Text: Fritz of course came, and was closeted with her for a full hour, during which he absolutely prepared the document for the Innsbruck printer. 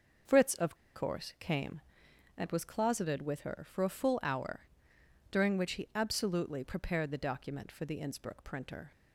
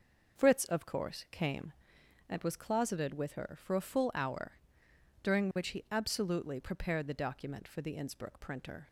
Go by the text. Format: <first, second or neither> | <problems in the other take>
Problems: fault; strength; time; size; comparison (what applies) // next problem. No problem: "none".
second | starts louder than the rest; noticeable; until 1.5 s; 6 dB // pauses between "of" and "course"; slight; at 0.7 s; 0.20 s long